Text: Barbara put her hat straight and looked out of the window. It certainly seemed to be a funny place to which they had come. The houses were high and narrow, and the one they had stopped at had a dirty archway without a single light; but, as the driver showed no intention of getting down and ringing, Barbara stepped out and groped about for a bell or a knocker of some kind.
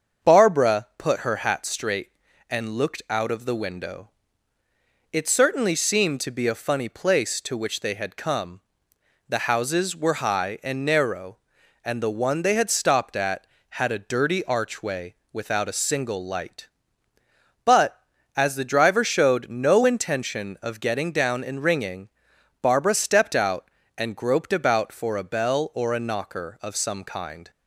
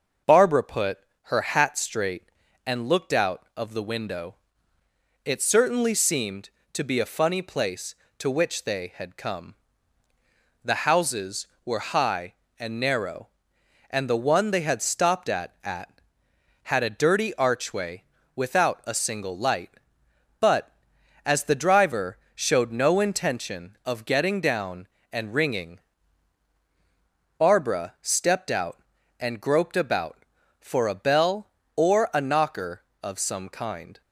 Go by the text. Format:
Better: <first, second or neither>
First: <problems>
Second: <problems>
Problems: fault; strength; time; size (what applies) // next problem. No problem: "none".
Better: first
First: starts louder than the rest; until 1.3 s; 7 dB // pauses between "archway" and "without"; slight; at 15.1 s; 0.16 s long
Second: starts louder than the rest; until 1.5 s; 6.5 dB // pauses between "put" and "her"; slight; at 0.9 s; 0.26 s long // says "at" twice; at 15.6 s // pauses between "archway" and "without"; slight; at 18.0 s; 0.31 s long // pauses between "driver" and "showed"; slight; at 22.1 s; 0.16 s long